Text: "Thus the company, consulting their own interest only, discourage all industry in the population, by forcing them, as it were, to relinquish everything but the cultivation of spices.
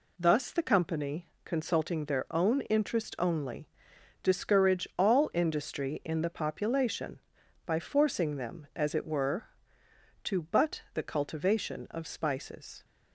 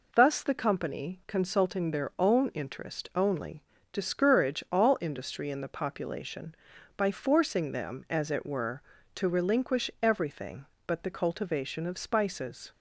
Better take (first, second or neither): second